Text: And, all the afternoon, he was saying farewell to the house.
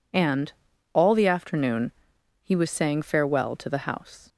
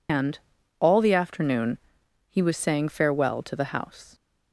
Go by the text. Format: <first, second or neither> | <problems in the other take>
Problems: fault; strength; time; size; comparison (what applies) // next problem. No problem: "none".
first | loses the start of "And"; at 0.0 s; 110 ms